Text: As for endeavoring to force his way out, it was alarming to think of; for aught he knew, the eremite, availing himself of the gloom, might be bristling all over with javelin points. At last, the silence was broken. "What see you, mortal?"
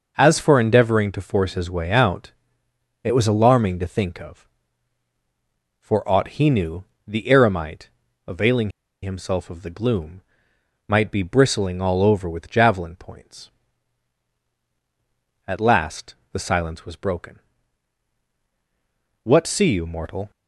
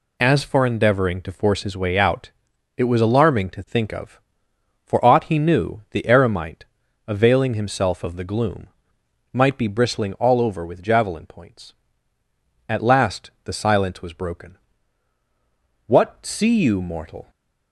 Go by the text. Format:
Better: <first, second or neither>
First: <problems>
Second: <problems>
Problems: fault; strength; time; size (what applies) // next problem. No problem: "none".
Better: second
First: pauses between "availing" and "himself"; slight; at 8.7 s; 0.31 s long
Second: none